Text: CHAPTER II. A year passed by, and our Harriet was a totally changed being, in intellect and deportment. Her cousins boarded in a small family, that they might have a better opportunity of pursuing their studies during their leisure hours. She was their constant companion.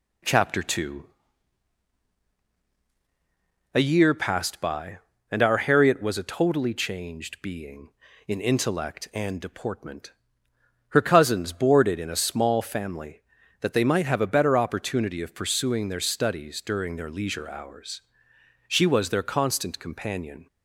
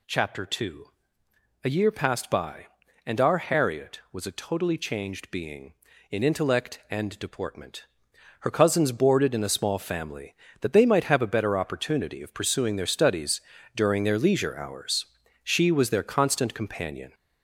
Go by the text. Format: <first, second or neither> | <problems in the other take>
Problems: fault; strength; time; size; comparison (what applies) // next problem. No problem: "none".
first | gets louder; noticeable; throughout; 4.5 dB // pauses between "studies" and "during"; slight; at 13.3 s; 0.34 s long